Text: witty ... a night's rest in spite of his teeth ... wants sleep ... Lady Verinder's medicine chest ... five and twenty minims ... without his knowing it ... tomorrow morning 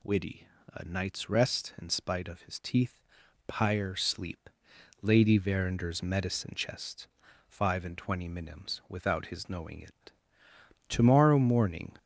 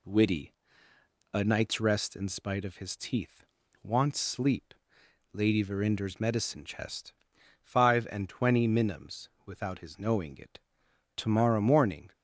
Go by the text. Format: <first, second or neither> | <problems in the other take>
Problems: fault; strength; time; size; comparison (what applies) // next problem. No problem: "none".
second | says "pyre" for "wants"; at 3.4 s